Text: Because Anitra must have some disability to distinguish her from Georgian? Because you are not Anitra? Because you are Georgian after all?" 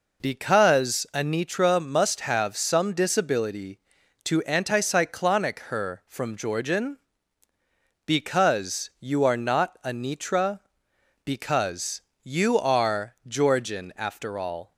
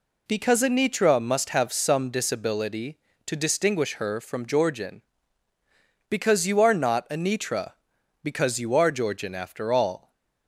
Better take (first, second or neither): second